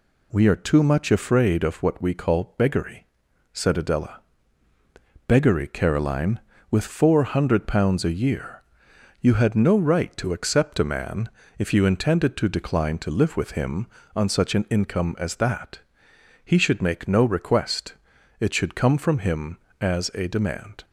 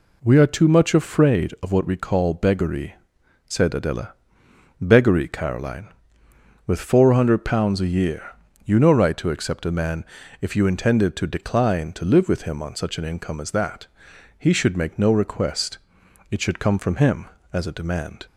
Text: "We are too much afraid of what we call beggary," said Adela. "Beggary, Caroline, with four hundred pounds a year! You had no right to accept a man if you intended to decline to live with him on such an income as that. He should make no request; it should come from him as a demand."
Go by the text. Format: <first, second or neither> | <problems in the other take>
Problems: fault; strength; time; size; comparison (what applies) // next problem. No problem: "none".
first | skips "had"; at 8.7 s // pauses between "man" and "if"; at 10.0 s; 0.38 s long; slight in the first